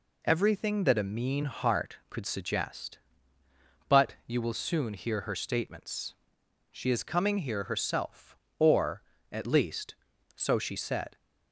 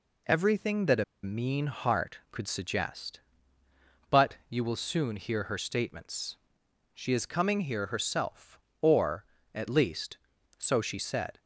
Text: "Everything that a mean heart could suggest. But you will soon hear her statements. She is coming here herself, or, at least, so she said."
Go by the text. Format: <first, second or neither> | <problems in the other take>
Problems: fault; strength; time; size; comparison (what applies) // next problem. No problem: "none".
first | pauses between "a" and "mean"; slight; at 1.0 s; 0.20 s long